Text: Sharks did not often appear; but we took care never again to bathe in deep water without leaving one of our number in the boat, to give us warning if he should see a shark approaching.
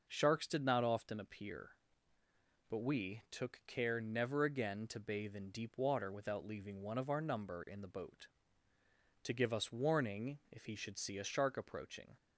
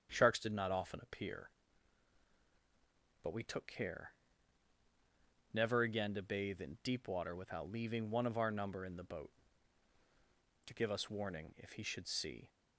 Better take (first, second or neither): first